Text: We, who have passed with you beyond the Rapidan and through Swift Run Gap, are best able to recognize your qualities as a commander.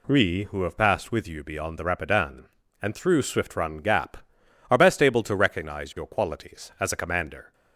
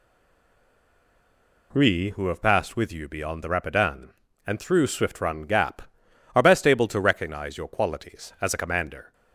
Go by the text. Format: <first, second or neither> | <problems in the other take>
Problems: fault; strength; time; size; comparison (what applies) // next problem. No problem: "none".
first | stays silent before the first word; noticeable; until 1.7 s; 1.7 s long